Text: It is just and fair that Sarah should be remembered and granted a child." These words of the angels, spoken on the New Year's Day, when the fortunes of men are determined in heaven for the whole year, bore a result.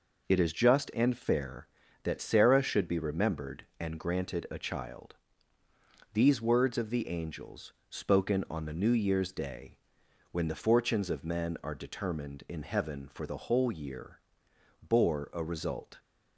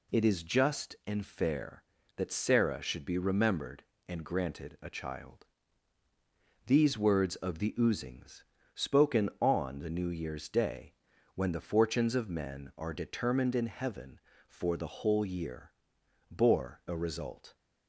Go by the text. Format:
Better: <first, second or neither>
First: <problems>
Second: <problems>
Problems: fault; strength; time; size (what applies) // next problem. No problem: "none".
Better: first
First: none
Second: says "oozings" for "angels"; at 7.7 s